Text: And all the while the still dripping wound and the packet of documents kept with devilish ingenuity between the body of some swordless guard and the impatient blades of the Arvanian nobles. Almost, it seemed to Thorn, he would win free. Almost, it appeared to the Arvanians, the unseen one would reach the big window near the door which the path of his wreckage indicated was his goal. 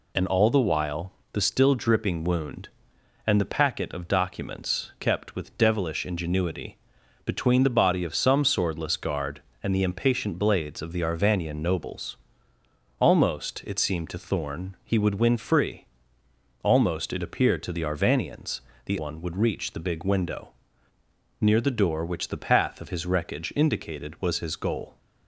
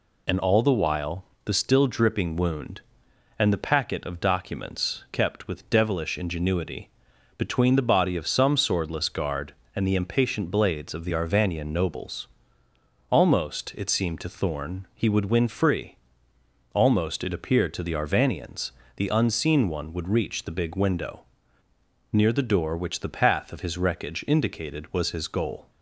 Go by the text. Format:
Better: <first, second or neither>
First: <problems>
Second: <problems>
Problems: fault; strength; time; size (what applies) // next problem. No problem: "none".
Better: second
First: pauses between "while" and "the"; slight; at 1.1 s; 0.22 s long // pauses between "ingenuity" and "between"; noticeable; at 6.7 s; 0.48 s long // skips "unseen"; at 18.9 s // pauses between "window" and "near"; noticeable; at 20.5 s; 0.88 s long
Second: pauses between "while" and "the"; slight; at 1.2 s; 0.22 s long // pauses between "ingenuity" and "between"; noticeable; at 6.8 s; 0.48 s long // pauses between "window" and "near"; noticeable; at 21.2 s; 0.88 s long